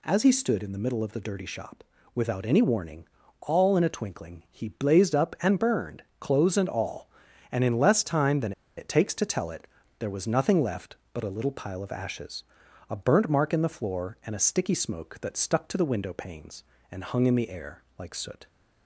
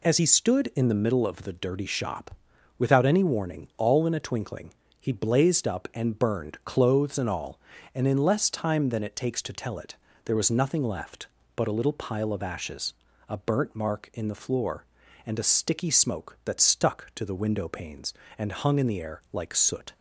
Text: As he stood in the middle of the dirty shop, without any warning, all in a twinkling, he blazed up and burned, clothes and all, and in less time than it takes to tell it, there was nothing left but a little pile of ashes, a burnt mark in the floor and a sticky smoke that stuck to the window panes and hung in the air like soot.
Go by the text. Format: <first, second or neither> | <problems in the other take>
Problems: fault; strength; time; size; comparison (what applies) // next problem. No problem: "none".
second | pauses between "than" and "it"; slight; at 8.5 s; 0.25 s long